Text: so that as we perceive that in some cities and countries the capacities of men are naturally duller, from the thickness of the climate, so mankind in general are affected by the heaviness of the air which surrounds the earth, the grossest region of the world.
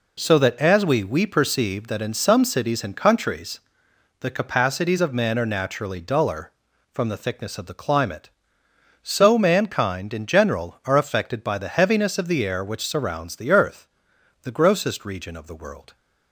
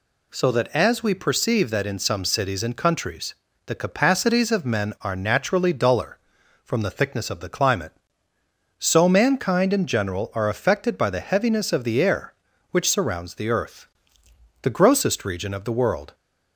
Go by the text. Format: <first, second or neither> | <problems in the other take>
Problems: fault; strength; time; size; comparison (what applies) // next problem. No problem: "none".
second | says "we" twice; at 1.0 s // pauses between "countries" and "the"; noticeable; at 3.6 s; 0.58 s long; slight in the second